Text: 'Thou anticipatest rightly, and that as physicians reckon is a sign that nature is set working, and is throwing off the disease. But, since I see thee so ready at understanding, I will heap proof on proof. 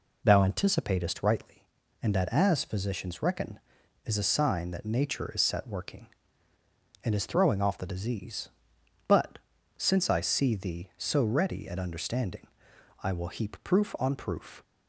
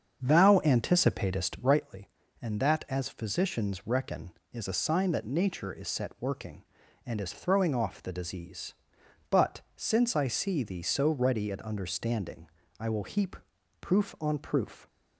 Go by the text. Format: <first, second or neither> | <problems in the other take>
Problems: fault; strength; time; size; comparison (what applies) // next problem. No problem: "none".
first | starts louder than the rest; until 1.9 s; 7 dB // pauses between "heap" and "proof"; at 13.3 s; 0.44 s long